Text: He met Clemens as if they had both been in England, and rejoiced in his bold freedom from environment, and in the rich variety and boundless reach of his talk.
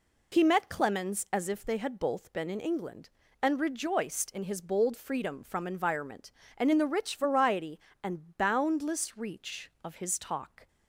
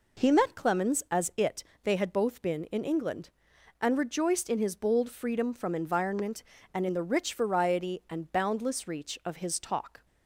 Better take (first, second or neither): first